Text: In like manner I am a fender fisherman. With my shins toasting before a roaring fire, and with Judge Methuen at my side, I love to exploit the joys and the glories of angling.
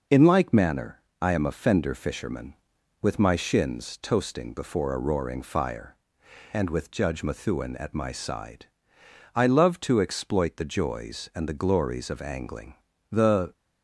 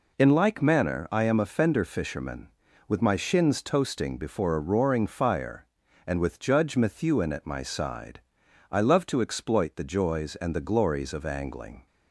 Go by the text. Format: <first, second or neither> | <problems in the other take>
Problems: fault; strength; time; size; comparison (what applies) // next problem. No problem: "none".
second | pauses between "manner" and "I"; slight; at 1.0 s; 0.18 s long // goes on to say "The"; slight; from 13.1 s on; 0.44 s long